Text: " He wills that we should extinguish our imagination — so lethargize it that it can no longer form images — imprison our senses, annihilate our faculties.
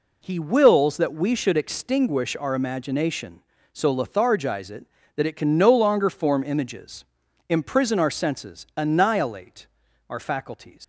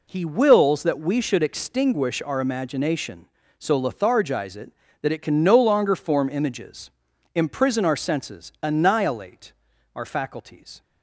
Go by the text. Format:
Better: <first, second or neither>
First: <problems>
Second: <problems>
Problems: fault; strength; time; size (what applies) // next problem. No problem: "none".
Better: second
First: pauses between "annihilate" and "our"; at 9.6 s; 0.42 s long // leaves "faculties" unfinished; at 10.8 s; 100 ms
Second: pauses between "annihilate" and "our"; at 9.5 s; 0.42 s long